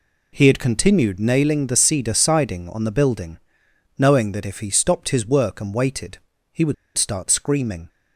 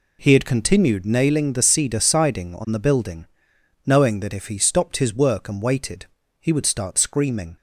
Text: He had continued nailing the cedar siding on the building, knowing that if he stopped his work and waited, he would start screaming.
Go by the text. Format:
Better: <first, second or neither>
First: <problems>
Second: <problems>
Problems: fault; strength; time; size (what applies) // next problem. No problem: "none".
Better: second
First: pauses between "would" and "start"; slight; at 6.7 s; 0.23 s long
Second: none